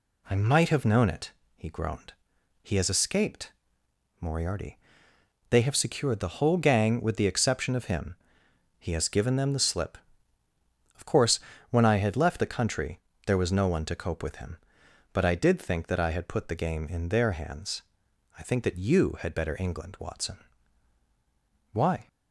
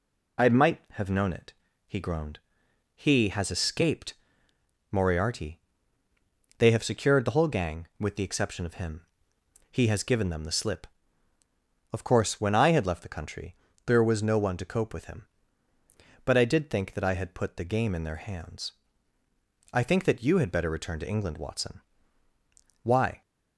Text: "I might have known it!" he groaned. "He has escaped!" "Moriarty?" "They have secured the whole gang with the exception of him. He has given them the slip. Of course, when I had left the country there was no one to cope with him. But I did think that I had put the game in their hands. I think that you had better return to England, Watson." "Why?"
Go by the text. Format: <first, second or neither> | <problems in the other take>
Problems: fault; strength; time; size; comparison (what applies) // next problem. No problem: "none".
second | pauses between "country" and "there"; slight; at 12.9 s; 0.26 s long; slight in the second // skips "return to"; at 19.5 s